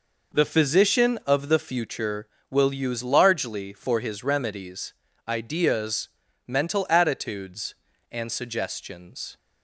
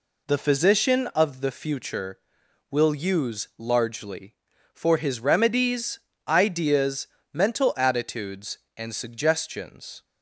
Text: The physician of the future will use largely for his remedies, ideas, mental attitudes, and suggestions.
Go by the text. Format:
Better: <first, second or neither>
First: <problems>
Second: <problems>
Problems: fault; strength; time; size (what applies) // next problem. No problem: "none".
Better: neither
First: none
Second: none